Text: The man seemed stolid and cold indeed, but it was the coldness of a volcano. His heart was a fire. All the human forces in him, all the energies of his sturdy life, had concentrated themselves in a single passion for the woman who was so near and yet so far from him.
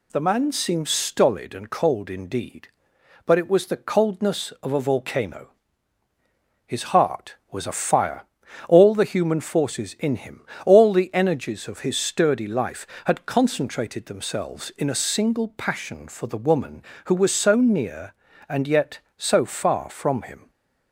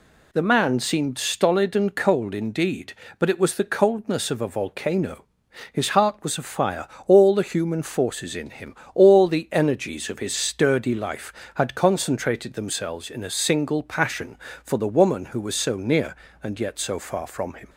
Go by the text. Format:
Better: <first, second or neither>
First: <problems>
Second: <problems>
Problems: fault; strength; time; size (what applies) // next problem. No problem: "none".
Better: neither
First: none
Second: none